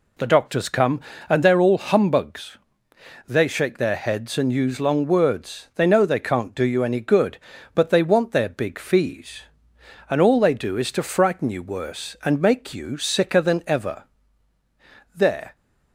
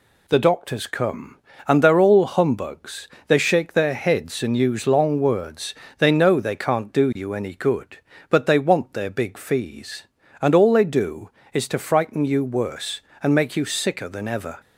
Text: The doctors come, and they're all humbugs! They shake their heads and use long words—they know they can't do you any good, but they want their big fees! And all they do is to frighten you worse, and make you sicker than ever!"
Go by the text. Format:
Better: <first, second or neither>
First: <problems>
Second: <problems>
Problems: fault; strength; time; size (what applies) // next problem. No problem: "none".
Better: second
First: goes on to say "There"; slight; from 15.1 s on; 0.42 s long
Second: none